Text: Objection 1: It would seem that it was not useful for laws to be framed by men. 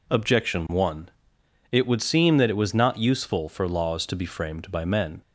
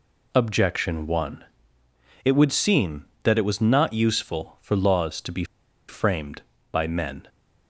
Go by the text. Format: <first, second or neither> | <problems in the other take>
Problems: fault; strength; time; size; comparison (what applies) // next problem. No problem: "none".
first | pauses between "be" and "framed"; at 5.4 s; 0.45 s long